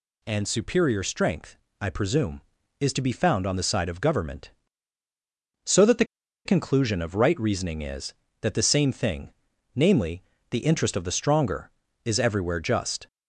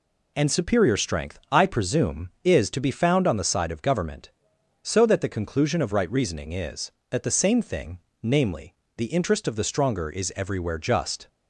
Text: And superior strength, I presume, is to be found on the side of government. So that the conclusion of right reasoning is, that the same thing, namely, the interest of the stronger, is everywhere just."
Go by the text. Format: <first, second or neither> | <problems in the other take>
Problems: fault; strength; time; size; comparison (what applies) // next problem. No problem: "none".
second | pauses between "the" and "conclusion"; at 6.0 s; 0.41 s long